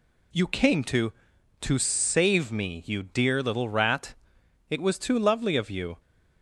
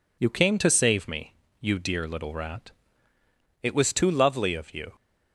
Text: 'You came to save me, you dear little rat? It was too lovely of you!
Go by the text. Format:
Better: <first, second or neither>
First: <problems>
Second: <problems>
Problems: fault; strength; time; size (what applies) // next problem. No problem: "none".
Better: second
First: says "to" twice; at 1.5 s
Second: none